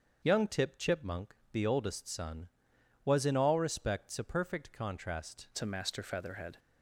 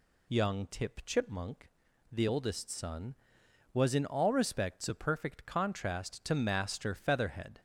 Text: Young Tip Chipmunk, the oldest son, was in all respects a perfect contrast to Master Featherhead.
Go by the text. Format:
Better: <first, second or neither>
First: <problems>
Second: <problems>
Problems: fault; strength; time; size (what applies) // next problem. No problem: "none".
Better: second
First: starts louder than the rest; until 1.2 s; 7 dB // changes voice at "to"; from 5.5 s on; 1.0 s long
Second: none